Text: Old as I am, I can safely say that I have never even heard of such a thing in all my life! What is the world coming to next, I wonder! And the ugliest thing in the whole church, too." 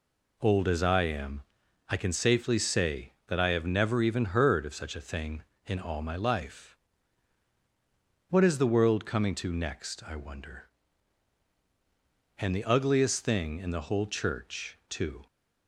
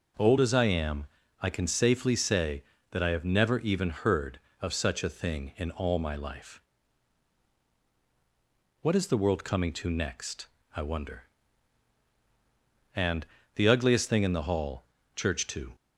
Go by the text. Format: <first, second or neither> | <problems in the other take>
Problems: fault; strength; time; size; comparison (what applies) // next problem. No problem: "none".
first | pauses between "And" and "the"; slight; at 13.2 s; 0.30 s long // says "hall" for "whole"; at 14.4 s